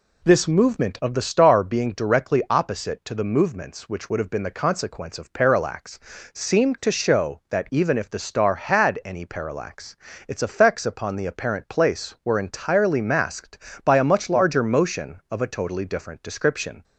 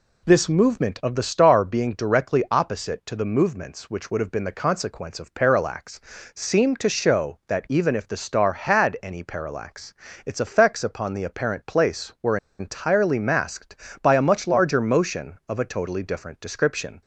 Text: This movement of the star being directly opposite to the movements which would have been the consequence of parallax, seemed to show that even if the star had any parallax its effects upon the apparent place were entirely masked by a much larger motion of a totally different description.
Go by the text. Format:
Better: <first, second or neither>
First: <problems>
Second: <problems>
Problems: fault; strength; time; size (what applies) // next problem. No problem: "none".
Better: first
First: pauses between "parallax" and "its"; slight; at 9.9 s; 0.32 s long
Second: pauses between "parallax" and "its"; slight; at 9.9 s; 0.32 s long // pauses between "were" and "entirely"; slight; at 12.3 s; 0.22 s long